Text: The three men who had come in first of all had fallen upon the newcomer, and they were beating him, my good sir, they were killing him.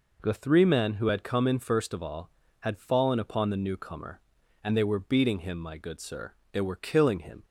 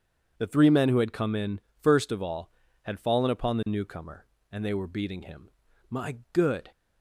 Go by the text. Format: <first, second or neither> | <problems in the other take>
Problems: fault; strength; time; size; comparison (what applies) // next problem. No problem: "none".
first | pauses between "in" and "first"; slight; at 1.5 s; 0.20 s long // pauses between "my" and "good"; slight; at 6.1 s; 0.16 s long // stops before "sir they were killing him"; at 6.7 s